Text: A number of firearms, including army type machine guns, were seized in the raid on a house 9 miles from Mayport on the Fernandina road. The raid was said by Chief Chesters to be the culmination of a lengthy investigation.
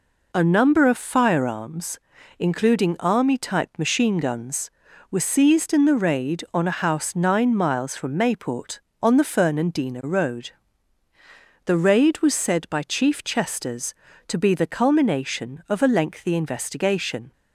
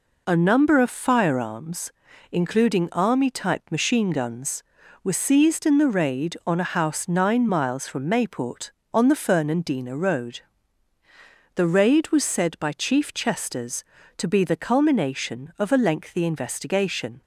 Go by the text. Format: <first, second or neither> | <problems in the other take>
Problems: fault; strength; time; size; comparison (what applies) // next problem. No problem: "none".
neither | none